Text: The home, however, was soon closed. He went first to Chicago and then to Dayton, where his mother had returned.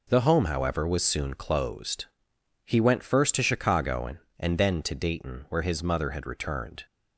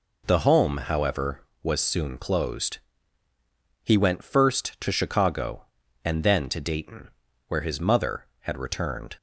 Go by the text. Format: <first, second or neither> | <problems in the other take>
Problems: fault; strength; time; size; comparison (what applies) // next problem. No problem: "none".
second | says "and" twice; at 4.4 s